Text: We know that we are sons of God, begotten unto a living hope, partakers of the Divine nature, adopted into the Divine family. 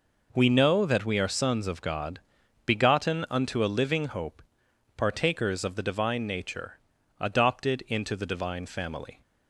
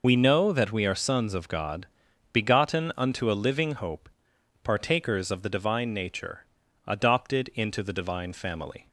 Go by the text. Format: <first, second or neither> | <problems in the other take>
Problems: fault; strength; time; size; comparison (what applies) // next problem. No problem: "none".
first | loses the start of "We"; at 0.0 s; 75 ms